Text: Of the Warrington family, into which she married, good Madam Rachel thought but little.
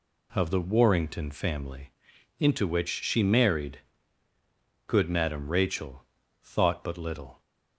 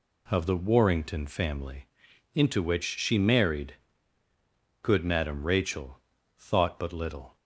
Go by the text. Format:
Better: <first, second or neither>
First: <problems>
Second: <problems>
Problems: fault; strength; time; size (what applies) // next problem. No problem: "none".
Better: neither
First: pauses between "Rachel" and "thought"; slight; at 6.0 s; 0.36 s long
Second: pauses between "Rachel" and "thought"; slight; at 5.9 s; 0.36 s long